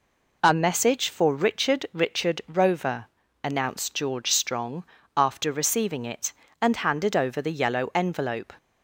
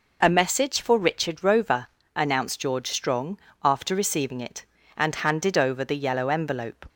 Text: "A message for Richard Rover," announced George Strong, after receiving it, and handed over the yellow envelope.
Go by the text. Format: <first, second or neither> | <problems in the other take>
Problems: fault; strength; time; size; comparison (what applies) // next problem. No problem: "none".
second | says "Richard" twice; at 1.9 s